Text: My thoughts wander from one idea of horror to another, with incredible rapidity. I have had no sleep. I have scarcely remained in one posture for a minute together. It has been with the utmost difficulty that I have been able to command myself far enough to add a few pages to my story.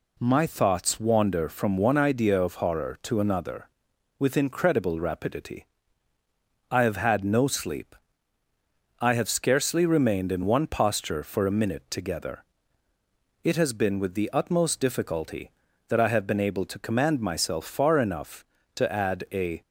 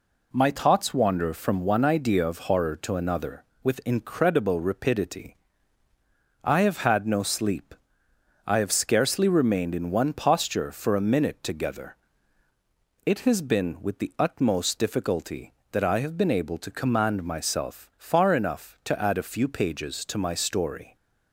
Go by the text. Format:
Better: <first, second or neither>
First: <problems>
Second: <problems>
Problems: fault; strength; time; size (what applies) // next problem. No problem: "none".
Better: second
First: stops before "few pages to my story"; at 19.6 s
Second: none